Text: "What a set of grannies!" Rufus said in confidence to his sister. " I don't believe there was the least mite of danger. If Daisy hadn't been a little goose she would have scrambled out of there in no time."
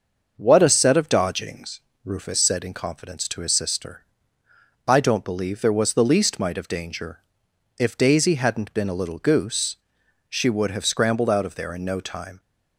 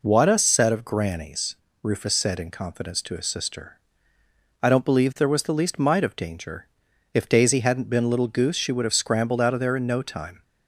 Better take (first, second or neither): second